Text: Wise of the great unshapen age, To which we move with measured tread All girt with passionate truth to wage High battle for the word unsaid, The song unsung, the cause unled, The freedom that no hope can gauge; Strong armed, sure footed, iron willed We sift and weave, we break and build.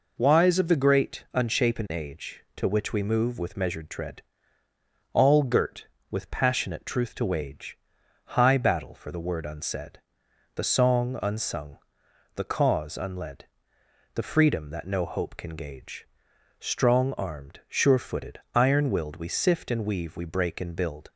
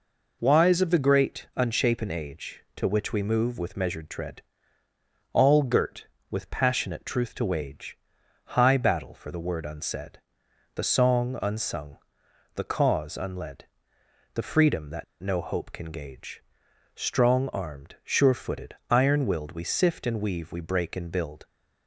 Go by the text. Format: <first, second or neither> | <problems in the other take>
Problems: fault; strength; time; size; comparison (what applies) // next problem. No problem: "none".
first | pauses between "tread" and "All"; noticeable; at 4.4 s; 0.92 s long; noticeable in the first // pauses between "wage" and "High"; noticeable; at 7.9 s; 0.48 s long; noticeable in the first // pauses between "that" and "no"; slight; at 15.0 s; 0.17 s long